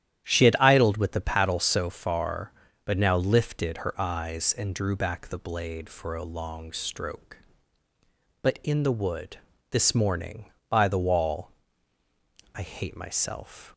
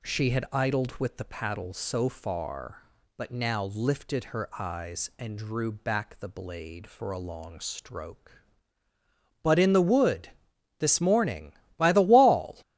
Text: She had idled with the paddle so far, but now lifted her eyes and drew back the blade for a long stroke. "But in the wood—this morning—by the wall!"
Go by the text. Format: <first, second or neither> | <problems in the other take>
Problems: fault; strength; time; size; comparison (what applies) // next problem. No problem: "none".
second | starts louder than the rest; strong; until 1.2 s; 10.5 dB // goes on to say "I hate myself"; noticeable; from 12.5 s on; 1.1 s long